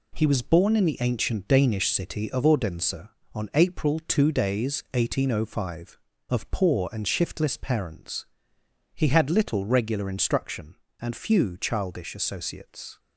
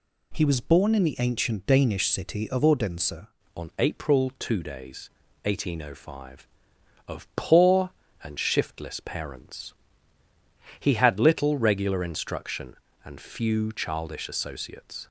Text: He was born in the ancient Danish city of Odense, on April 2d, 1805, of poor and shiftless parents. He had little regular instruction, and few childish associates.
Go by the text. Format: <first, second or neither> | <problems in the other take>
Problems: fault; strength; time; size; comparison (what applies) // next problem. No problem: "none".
first | changes voice at "on"; from 3.5 s on; 11.5 s long